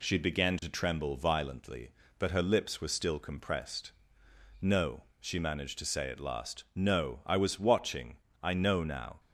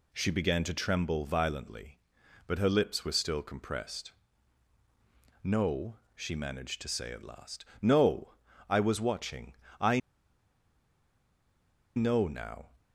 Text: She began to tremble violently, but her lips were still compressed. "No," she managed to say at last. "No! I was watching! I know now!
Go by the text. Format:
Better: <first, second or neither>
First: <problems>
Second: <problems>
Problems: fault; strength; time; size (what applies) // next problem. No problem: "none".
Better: first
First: none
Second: pauses between "I" and "know"; strong; at 9.9 s; 1.9 s long